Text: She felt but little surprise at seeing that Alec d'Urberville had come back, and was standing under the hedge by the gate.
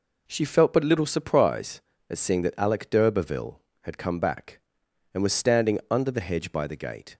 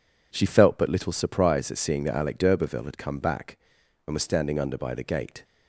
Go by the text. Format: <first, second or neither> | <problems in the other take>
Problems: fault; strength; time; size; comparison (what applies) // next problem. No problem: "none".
first | skips "the hedge"; at 4.7 s